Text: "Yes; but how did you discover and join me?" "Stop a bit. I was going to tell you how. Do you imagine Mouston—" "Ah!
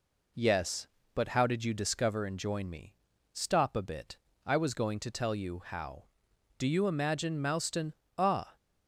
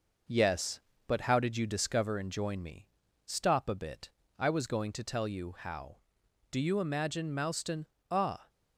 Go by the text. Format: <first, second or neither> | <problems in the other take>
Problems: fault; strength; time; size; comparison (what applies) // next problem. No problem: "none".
first | gets quieter; slight; throughout; 3 dB